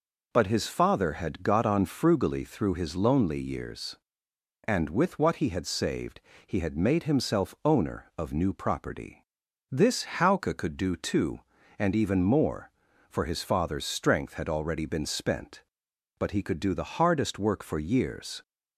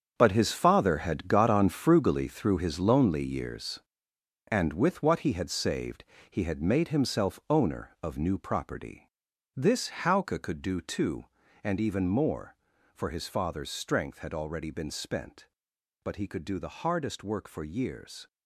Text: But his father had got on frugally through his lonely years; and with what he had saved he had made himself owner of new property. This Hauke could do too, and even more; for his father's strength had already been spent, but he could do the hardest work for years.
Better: first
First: pauses between "saved" and "he"; slight; at 6.1 s; 0.26 s long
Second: gets quieter; strong; throughout; 11.5 dB // pauses between "saved" and "he"; slight; at 6.0 s; 0.26 s long

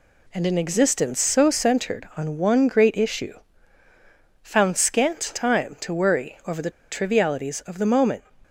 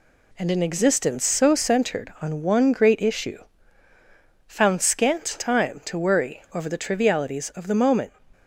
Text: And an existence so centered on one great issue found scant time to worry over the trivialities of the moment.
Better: second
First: pauses between "issue" and "found"; at 3.3 s; 1.0 s long // pauses between "the" and "trivialities"; slight; at 6.6 s; 0.20 s long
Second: pauses between "issue" and "found"; at 3.4 s; 1.0 s long

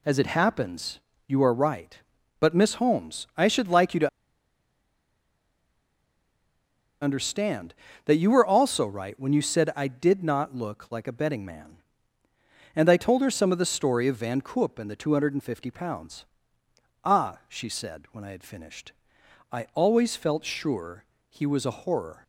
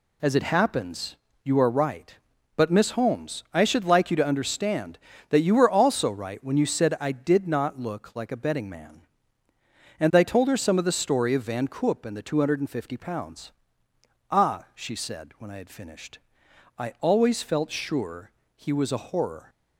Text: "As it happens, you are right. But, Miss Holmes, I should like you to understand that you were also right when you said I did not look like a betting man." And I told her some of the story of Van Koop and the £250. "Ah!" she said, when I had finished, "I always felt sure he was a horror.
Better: second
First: pauses between "to" and "understand"; strong; at 4.0 s; 2.9 s long // pauses between "sure" and "he"; slight; at 21.0 s; 0.24 s long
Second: pauses between "sure" and "he"; slight; at 18.3 s; 0.24 s long

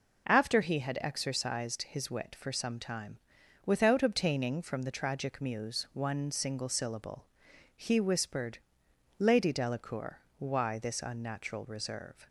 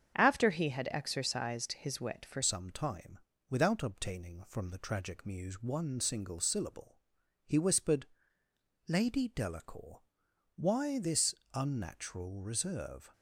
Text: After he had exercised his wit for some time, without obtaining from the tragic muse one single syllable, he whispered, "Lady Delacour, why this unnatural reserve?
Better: first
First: none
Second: starts louder than the rest; strong; until 1.2 s; 7.5 dB // changes voice at "some"; from 2.4 s on; 10.7 s long // pauses between "this" and "unnatural"; slight; at 11.3 s; 0.20 s long

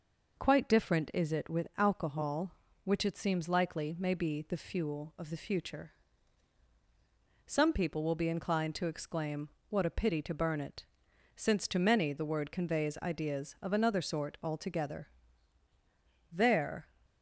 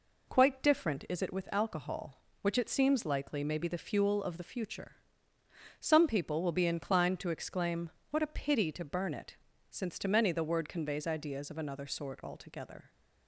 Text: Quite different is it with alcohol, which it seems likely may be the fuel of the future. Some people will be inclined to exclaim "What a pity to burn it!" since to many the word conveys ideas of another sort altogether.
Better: second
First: pauses between "exclaim" and "What"; slight; at 9.4 s; 0.20 s long // goes on to say "There"; from 16.3 s on; 0.56 s long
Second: pauses between "exclaim" and "What"; slight; at 7.8 s; 0.22 s long

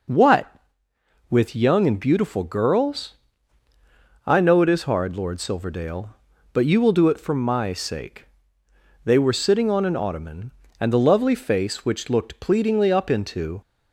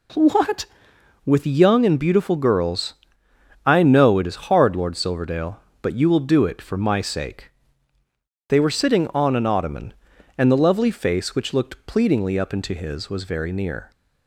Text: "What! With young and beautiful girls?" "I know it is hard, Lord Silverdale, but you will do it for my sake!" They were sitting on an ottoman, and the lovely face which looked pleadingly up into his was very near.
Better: second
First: stops before "his was very near"; at 13.6 s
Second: none

